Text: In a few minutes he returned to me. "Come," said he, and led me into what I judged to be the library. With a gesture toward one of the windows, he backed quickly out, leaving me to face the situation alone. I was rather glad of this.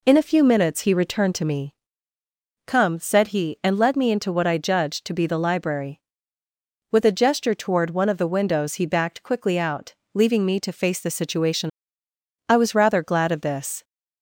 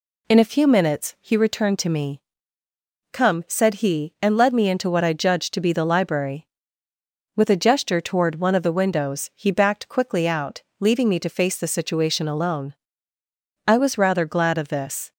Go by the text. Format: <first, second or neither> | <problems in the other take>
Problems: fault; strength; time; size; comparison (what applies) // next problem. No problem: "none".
second | skips "alone"; at 12.0 s